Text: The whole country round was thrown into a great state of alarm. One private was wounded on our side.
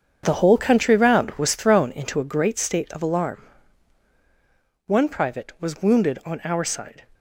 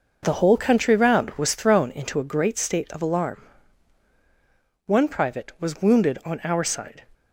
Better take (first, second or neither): second